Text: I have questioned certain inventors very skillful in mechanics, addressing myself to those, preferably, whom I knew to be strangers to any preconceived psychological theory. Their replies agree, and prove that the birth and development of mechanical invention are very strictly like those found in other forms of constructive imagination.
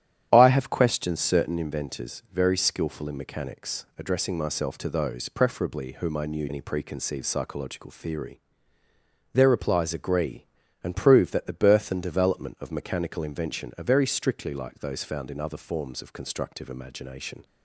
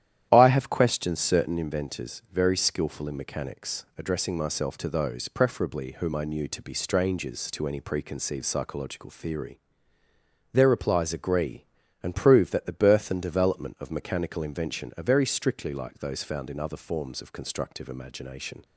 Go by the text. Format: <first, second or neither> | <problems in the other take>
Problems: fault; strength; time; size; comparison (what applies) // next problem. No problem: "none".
second | starts louder than the rest; strong; until 1.3 s; 10 dB; strong in the second // skips "to be strangers to"; at 6.4 s